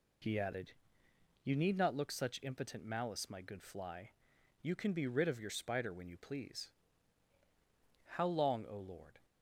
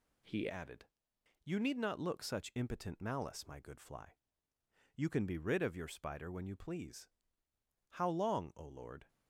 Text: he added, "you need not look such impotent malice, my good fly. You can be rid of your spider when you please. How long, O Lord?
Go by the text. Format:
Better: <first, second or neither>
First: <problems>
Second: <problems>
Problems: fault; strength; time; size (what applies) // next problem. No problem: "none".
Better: first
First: none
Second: changes voice at "added"; from 0.4 s on; 8.6 s long